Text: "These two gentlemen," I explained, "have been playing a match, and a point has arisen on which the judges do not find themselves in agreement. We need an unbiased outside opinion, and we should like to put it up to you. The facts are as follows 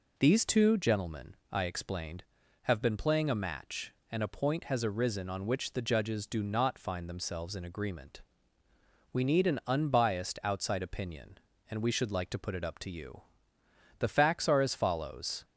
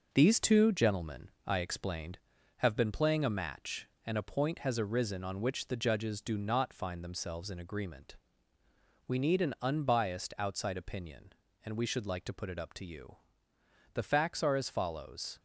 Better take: first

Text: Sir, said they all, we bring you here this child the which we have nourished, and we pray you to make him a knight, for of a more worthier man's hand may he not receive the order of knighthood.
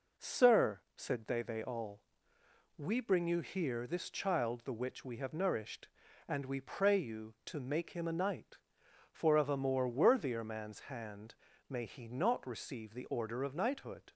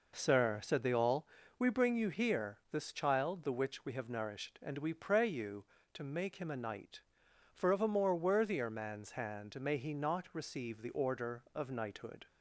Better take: second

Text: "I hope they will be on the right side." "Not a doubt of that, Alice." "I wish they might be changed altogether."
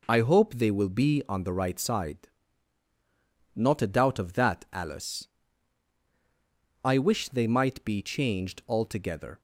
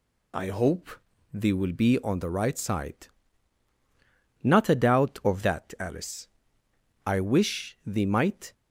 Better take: first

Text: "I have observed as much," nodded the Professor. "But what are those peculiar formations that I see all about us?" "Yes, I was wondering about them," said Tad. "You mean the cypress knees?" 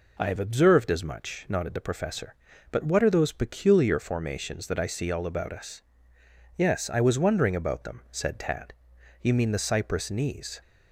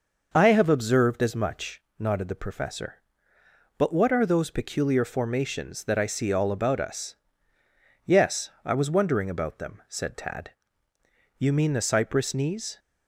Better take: neither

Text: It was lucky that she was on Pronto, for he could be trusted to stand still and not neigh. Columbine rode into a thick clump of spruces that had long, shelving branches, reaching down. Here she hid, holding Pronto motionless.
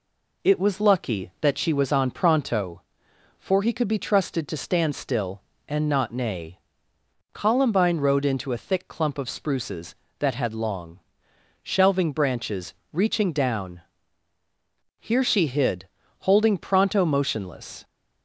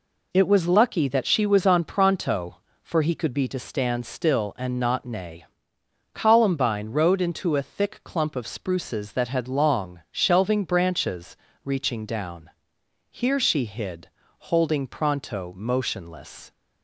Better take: first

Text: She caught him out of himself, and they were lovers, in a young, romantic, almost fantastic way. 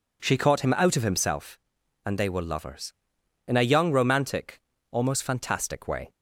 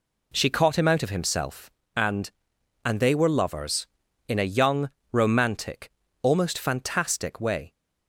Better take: first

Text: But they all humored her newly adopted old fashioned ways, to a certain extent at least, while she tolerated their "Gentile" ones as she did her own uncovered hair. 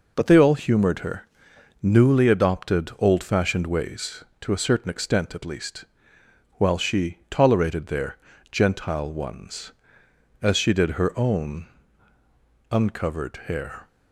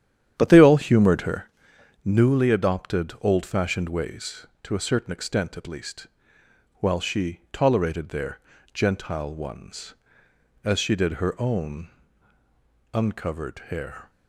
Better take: first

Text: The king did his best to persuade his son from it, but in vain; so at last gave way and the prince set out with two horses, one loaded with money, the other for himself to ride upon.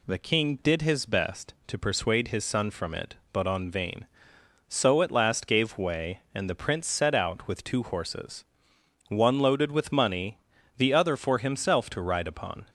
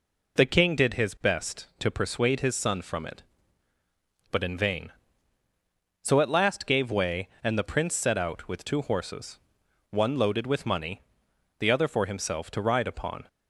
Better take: second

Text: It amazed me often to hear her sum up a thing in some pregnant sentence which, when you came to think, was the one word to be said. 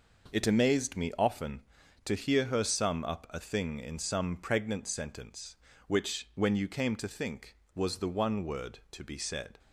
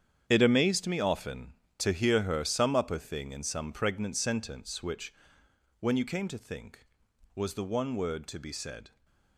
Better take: first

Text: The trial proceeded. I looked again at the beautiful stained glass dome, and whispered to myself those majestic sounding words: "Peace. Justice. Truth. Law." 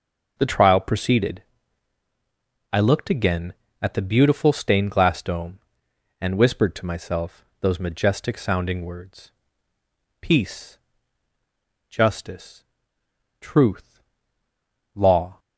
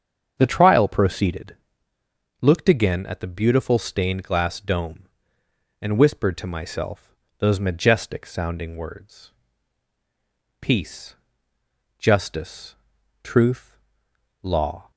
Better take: first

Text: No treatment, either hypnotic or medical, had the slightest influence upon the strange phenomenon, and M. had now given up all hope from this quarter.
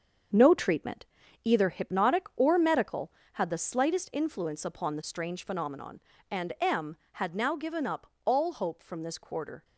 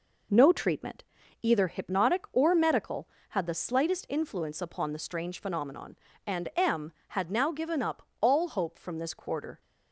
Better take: second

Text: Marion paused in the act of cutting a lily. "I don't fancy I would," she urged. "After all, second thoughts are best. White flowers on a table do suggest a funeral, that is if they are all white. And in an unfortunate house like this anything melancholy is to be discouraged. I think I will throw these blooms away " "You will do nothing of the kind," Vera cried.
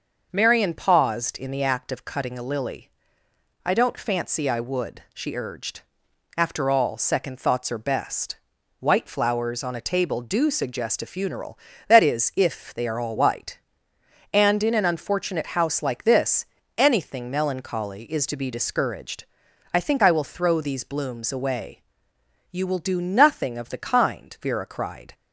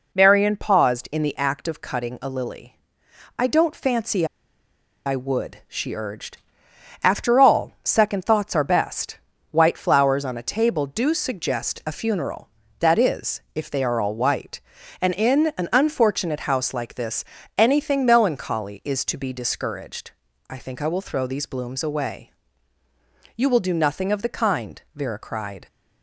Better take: first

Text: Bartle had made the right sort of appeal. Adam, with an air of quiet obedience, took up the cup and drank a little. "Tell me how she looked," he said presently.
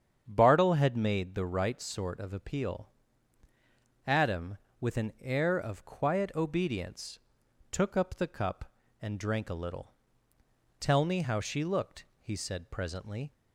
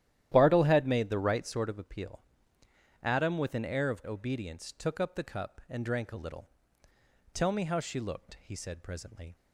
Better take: first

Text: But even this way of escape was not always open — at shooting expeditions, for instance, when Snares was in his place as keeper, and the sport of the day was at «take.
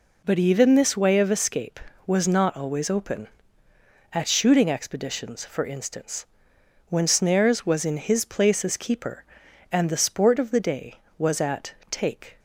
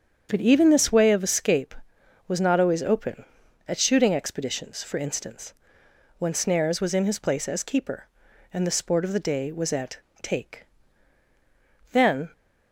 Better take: first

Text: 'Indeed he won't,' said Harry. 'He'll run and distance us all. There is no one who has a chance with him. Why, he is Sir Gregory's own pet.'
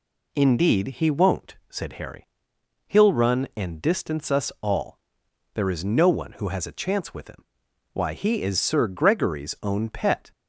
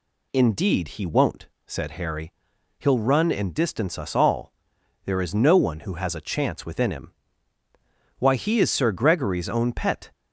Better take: first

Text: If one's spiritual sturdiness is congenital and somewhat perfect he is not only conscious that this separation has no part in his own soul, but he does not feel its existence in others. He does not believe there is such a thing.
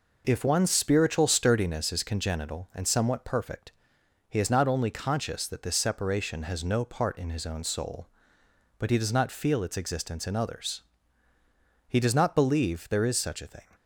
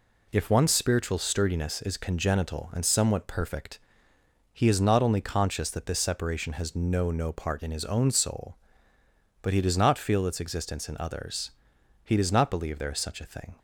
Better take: first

